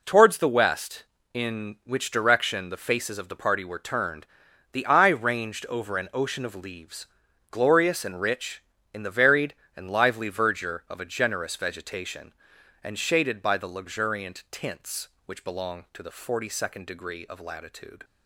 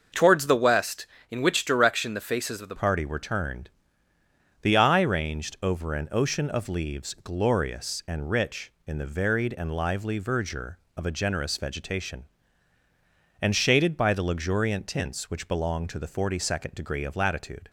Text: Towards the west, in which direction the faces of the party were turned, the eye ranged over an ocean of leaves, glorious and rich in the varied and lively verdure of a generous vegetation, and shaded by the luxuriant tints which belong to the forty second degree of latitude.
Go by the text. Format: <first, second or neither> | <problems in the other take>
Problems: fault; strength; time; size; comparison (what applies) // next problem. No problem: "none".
first | starts louder than the rest; noticeable; until 1.3 s; 6 dB // changes voice at "party"; from 2.7 s on; 14.9 s long